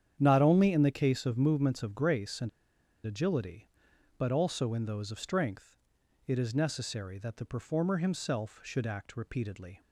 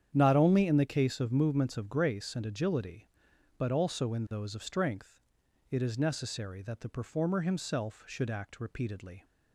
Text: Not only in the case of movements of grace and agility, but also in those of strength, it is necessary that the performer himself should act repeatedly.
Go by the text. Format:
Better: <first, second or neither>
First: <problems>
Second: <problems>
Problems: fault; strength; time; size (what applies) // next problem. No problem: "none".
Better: second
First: starts louder than the rest; strong; until 1.2 s; 9 dB // pauses between "and" and "agility"; noticeable; at 2.4 s; 0.56 s long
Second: starts louder than the rest; strong; until 1.1 s; 9 dB